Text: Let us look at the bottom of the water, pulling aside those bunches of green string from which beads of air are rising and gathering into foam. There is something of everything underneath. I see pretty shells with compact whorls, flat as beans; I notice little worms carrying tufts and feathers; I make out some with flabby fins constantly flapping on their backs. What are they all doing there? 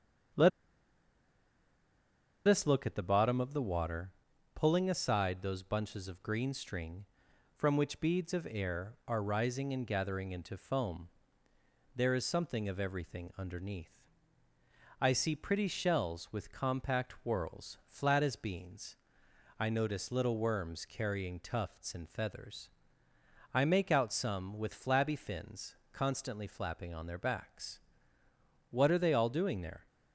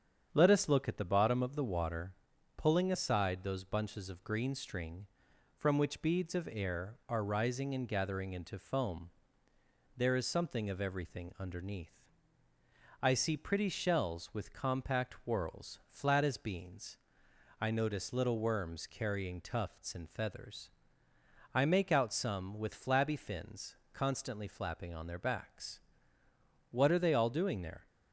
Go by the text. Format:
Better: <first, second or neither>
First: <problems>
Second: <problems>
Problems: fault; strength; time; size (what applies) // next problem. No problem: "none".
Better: second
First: starts louder than the rest; strong; until 3.3 s; 7.5 dB // pauses between "Let" and "us"; strong; at 0.4 s; 1.9 s long // pauses between "fins" and "constantly"; slight; at 25.7 s; 0.18 s long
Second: starts louder than the rest; strong; until 1.3 s; 8 dB // pauses between "fins" and "constantly"; slight; at 23.7 s; 0.18 s long